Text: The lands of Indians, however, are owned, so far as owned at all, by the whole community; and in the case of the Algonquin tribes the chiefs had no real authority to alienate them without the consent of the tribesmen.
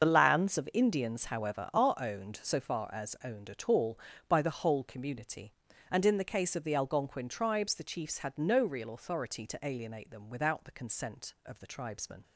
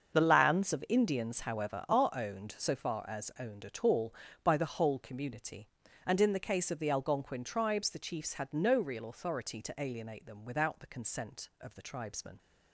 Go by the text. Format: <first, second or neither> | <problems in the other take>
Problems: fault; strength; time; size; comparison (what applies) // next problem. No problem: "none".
second | loses the start of "The"; at 0.0 s; 35 ms // starts louder than the rest; until 1.0 s; 6.5 dB; also in the second